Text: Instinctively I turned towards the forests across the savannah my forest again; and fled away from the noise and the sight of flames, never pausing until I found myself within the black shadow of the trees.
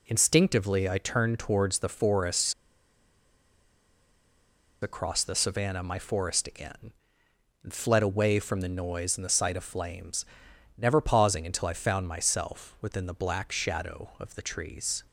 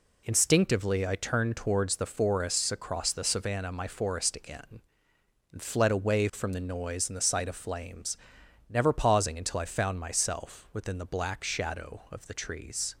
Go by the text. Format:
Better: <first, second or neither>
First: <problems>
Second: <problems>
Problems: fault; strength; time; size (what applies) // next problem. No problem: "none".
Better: second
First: pauses between "forests" and "across"; strong; at 2.5 s; 2.2 s long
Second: none